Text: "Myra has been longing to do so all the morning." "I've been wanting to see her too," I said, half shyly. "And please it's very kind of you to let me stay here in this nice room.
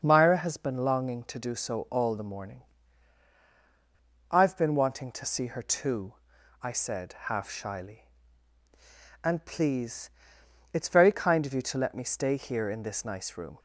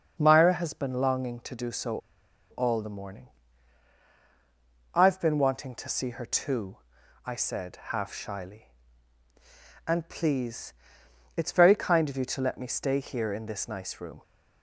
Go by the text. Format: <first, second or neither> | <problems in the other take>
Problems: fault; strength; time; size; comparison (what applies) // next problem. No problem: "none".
first | starts louder than the rest; until 1.2 s; 6 dB; also in the first // pauses between "so" and "all"; noticeable; at 1.9 s; 0.52 s long // pauses between "please" and "it's"; noticeable; at 10.7 s; 0.64 s long; noticeable in the first